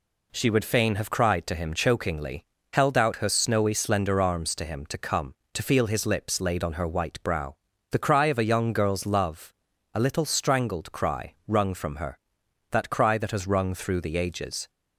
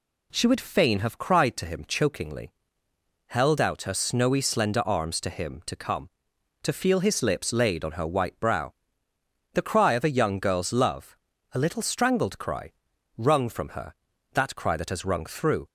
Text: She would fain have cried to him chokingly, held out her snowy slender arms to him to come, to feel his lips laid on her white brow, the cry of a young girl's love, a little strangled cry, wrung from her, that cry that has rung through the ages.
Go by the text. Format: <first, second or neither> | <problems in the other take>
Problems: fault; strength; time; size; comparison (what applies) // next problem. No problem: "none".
first | stops before "the ages"; at 15.6 s